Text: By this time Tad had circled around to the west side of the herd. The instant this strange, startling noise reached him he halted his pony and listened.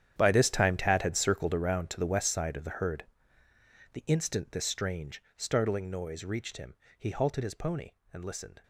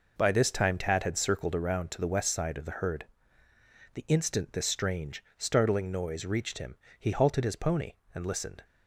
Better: second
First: gets quieter; strong; throughout; 15 dB // pauses between "him" and "he"; slight; at 6.7 s; 0.24 s long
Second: pauses between "him" and "he"; slight; at 6.7 s; 0.24 s long

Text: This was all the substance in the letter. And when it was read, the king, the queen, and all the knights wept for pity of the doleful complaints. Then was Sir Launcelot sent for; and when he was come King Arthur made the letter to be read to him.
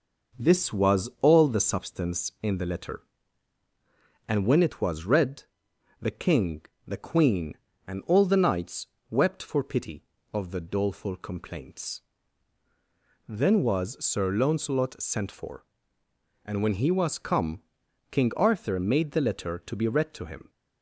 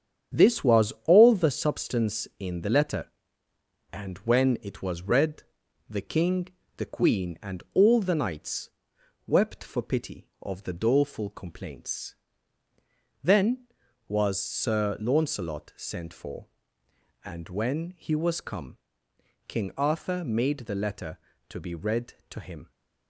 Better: first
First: pauses between "knights" and "wept"; slight; at 8.8 s; 0.22 s long // pauses between "come" and "King"; noticeable; at 17.6 s; 0.48 s long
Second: gets quieter; strong; throughout; 7.5 dB // pauses between "knights" and "wept"; noticeable; at 8.7 s; 0.56 s long // pauses between "come" and "King"; noticeable; at 18.7 s; 0.70 s long

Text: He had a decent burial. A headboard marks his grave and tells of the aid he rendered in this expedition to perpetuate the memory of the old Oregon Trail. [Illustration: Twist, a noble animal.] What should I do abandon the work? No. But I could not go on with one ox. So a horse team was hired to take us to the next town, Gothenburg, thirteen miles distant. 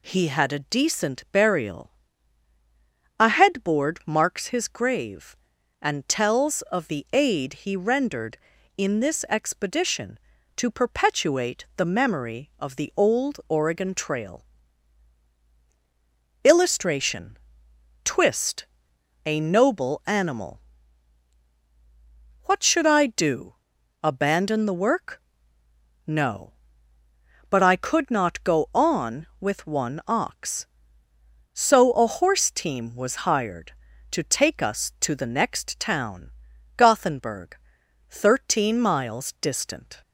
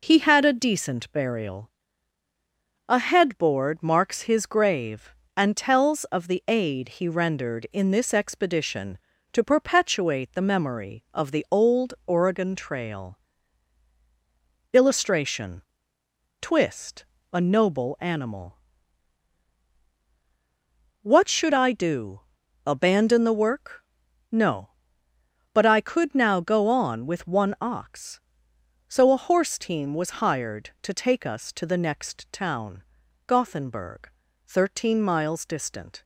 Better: first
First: pauses between "do" and "abandon"; noticeable; at 23.5 s; 0.46 s long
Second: pauses between "do" and "abandon"; noticeable; at 22.1 s; 0.48 s long // says "now" for "not"; at 26.1 s

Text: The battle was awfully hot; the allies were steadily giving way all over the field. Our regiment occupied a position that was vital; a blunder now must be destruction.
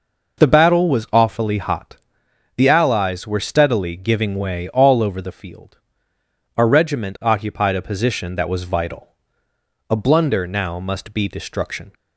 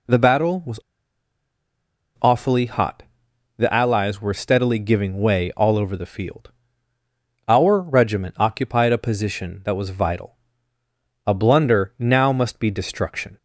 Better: first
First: none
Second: pauses between "was" and "awfully"; strong; at 0.7 s; 1.4 s long

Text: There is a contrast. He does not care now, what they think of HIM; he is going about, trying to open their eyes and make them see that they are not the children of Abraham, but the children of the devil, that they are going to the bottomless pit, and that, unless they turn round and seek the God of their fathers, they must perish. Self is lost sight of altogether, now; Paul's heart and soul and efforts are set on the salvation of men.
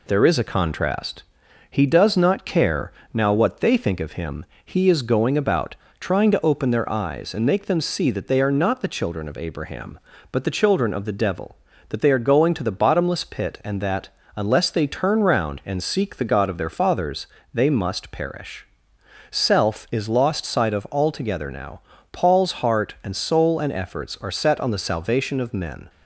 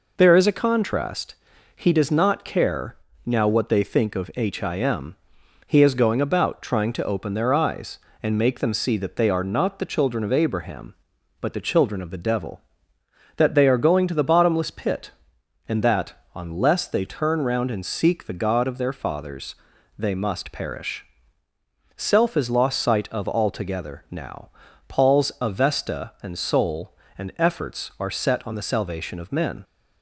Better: first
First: pauses between "care" and "now"; slight; at 2.9 s; 0.20 s long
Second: pauses between "care" and "now"; slight; at 2.9 s; 0.30 s long // says "avesta" for "heart"; at 25.4 s

